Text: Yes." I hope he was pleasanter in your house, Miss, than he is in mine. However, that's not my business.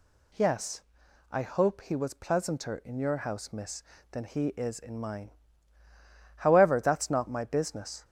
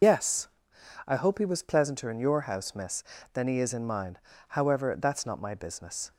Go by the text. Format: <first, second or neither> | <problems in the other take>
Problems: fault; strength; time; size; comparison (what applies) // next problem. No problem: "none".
first | loses the start of "Yes"; at 0.0 s; 95 ms